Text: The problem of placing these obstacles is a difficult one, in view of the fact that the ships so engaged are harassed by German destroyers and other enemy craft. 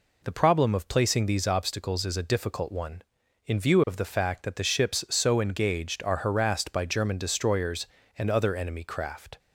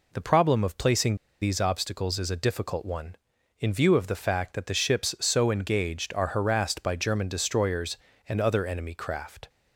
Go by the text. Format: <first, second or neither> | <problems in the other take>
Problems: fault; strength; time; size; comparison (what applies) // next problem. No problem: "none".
first | pauses between "placing" and "these"; slight; at 1.1 s; 0.27 s long